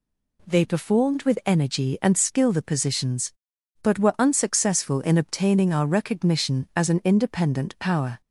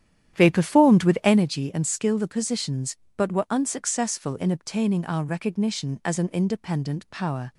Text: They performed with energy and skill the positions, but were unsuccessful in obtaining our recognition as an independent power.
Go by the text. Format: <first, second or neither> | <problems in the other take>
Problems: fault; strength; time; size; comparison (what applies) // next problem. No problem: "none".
first | starts louder than the rest; strong; until 1.5 s; 10.5 dB